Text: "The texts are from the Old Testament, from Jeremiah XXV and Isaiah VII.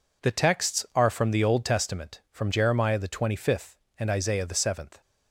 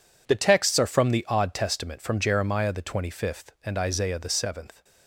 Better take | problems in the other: first | says "Odd" for "Old"; at 1.2 s

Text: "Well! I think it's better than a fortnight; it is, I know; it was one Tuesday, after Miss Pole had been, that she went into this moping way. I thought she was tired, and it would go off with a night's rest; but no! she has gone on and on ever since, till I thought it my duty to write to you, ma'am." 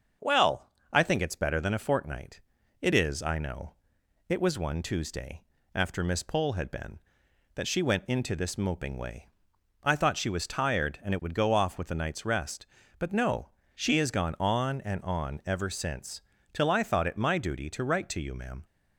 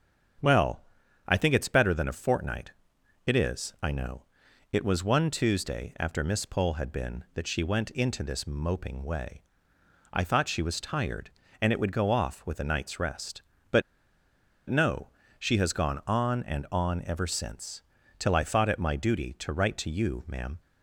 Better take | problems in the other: first | starts louder than the rest; strong; until 1.8 s; 7.5 dB; also in the first // pauses between "but" and "no"; noticeable; at 13.8 s; 0.86 s long

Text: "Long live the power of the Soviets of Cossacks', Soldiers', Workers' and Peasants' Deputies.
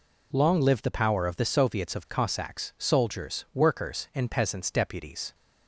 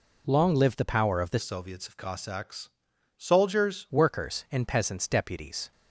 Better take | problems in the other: first | changes voice from "Soviets" to "Soldiers"; from 1.3 to 3.8 s; 2.5 s long

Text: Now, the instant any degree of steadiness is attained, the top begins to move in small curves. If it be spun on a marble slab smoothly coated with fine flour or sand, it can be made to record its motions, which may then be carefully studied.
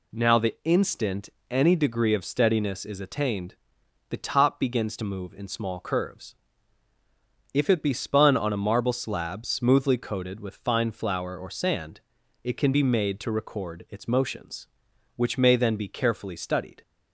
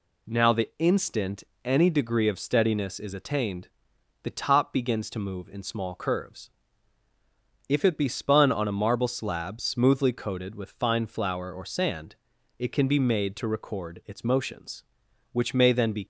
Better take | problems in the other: first | pauses between "instant" and "any"; slight; at 1.4 s; 0.20 s long; slight in the first // stops before "carefully studied"; at 16.0 s

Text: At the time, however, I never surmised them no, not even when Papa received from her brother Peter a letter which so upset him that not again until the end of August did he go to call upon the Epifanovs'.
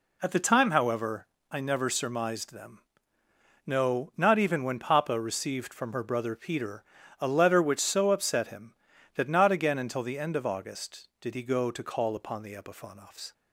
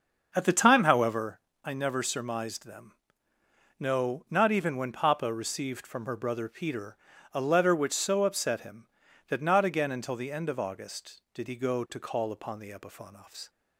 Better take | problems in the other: first | starts louder than the rest; until 1.3 s; 6.5 dB // pauses between "them" and "no"; noticeable; at 2.9 s; 0.90 s long; noticeable in the first // pauses between "Peter" and "a"; slight; at 6.9 s; 0.34 s long; slight in the first

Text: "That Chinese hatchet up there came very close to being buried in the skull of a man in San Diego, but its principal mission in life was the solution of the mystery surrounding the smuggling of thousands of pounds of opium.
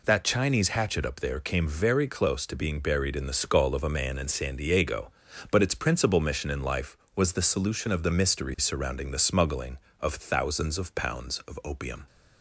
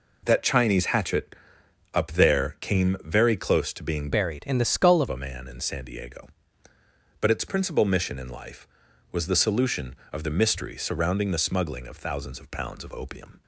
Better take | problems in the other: first | pauses between "hatchet" and "up"; noticeable; at 1.3 s; 0.56 s long // changes voice from "buried" to "of"; from 4.1 to 5.0 s; 0.9 s long

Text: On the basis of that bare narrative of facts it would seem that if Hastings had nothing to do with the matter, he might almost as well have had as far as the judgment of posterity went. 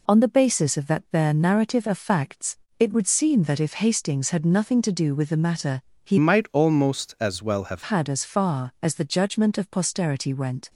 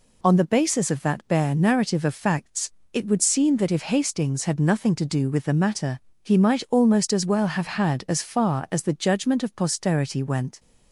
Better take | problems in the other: second | pauses between "facts" and "it"; slight; at 2.5 s; 0.20 s long; slight in the second // changes voice from "might" to "have"; from 6.1 to 7.8 s; 1.7 s long

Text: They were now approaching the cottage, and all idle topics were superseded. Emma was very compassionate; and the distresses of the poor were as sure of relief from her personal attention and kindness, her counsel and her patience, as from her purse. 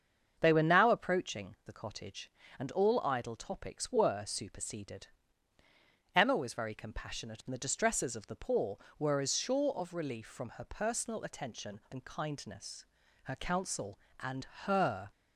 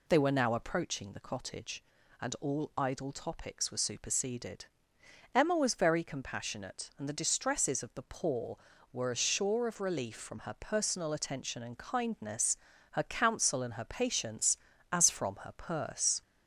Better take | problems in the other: second | starts louder than the rest; until 1.4 s; 7 dB // pauses between "and" and "her"; slight; at 14.4 s; 0.18 s long // stops before "patience as from her purse"; at 15.1 s

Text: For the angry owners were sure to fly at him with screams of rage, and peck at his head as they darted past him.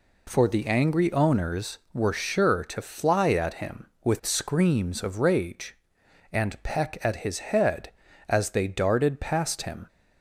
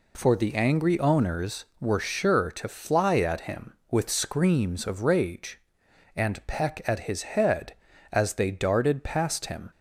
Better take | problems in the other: neither | none

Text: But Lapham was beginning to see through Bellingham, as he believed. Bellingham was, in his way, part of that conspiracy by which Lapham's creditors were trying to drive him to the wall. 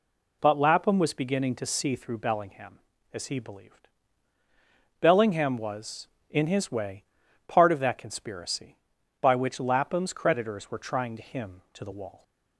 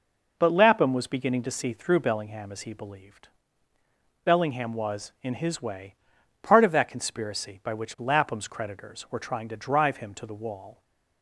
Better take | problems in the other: second | skips "drive"; at 11.2 s

